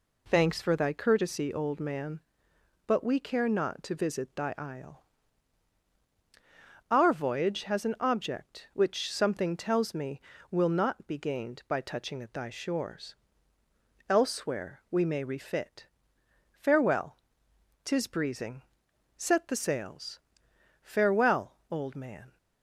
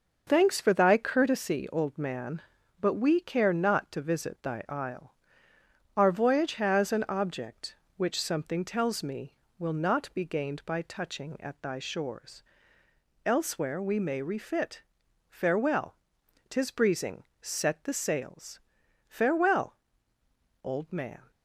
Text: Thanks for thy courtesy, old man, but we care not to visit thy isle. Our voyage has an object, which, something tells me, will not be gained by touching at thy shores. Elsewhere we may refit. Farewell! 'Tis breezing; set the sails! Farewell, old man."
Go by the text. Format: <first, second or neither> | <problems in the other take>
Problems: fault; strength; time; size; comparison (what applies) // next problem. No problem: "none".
neither | none